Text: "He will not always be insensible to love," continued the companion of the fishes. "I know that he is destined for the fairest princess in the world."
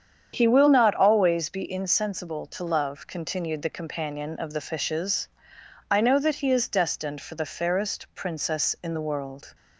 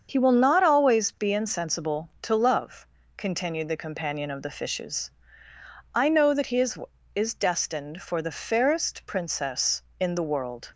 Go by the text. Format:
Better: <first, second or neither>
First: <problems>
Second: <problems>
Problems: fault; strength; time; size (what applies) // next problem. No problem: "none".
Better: first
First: starts louder than the rest; strong; until 1.3 s; 8 dB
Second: starts louder than the rest; until 1.1 s; 7 dB // says "is" twice; at 7.1 s